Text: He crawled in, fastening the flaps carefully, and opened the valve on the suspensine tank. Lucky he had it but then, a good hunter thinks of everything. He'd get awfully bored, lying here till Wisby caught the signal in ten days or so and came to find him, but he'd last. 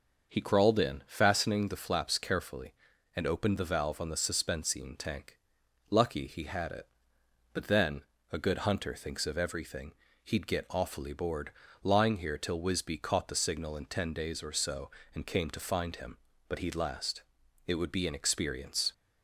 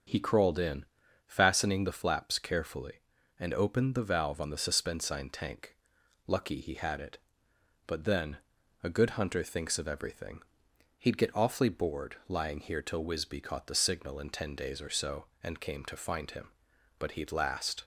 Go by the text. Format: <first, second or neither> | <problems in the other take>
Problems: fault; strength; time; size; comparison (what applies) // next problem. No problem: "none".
second | starts louder than the rest; noticeable; until 1.3 s; 6 dB; also in the second // goes on to say "It would be an experience"; noticeable; from 17.6 s on; 1.2 s long